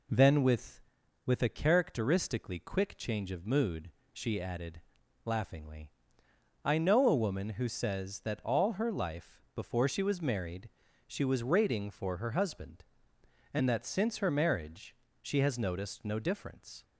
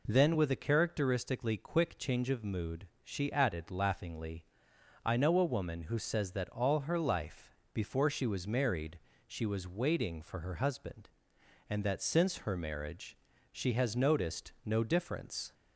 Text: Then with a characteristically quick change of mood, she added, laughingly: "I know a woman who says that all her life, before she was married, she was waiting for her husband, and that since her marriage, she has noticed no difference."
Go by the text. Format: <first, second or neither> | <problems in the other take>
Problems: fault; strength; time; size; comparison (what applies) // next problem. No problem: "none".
second | says "with" twice; at 1.2 s